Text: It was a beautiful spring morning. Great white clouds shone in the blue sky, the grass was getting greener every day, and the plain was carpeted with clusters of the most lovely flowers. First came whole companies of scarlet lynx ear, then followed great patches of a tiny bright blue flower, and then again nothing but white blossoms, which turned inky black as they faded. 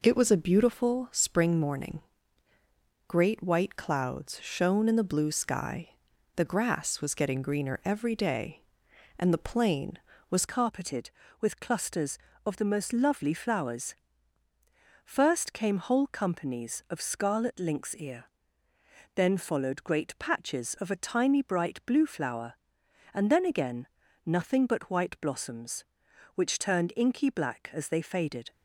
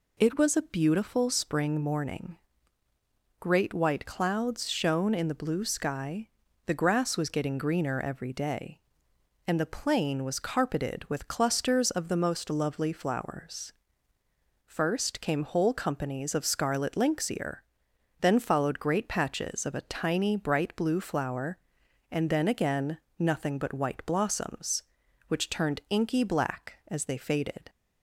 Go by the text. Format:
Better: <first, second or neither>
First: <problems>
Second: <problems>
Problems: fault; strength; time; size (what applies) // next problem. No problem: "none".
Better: second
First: changes voice at "carpeted"; from 10.4 s on; 18.1 s long // pauses between "again" and "nothing"; at 23.8 s; 0.40 s long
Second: pauses between "again" and "nothing"; slight; at 22.9 s; 0.22 s long